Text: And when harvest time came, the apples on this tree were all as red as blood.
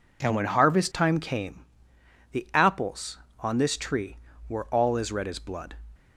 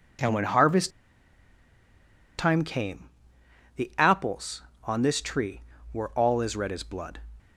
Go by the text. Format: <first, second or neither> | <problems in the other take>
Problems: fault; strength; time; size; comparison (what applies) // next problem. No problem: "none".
first | pauses between "harvest" and "time"; strong; at 0.9 s; 1.4 s long